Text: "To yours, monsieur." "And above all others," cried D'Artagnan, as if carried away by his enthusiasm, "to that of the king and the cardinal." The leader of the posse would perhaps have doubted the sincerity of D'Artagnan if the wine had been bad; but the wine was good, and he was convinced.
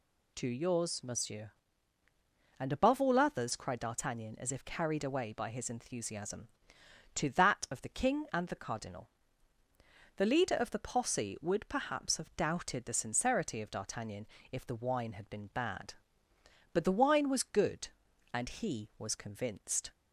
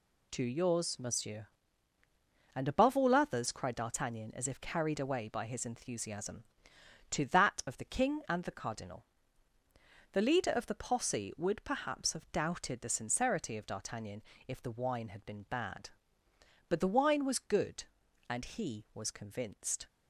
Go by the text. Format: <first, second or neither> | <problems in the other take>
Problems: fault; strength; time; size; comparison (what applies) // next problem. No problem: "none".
first | gets quieter; strong; throughout; 7.5 dB // pauses between "D'Artagnan" and "if"; slight; at 14.2 s; 0.26 s long; slight in the first